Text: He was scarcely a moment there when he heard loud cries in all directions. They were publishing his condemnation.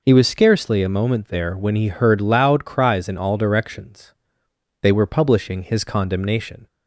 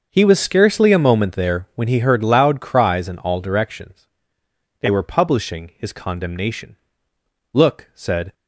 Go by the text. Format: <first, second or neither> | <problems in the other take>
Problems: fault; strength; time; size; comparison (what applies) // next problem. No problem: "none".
first | starts louder than the rest; until 1.1 s; 6.5 dB // goes on to say "Look said"; noticeable; from 7.5 s on; 0.80 s long